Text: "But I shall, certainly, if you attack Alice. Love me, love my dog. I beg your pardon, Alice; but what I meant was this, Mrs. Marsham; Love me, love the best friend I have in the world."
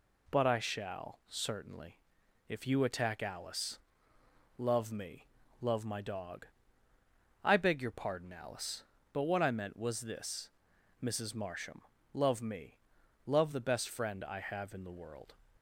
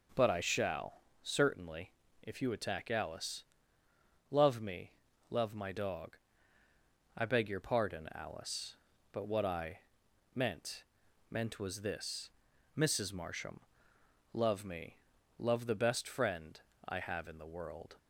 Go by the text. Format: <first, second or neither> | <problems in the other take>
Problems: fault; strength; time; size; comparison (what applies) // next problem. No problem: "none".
first | pauses between "I" and "meant"; noticeable; at 9.7 s; 0.54 s long // says "meant" twice; at 11.2 s // pauses between "friend" and "I"; slight; at 16.5 s; 0.30 s long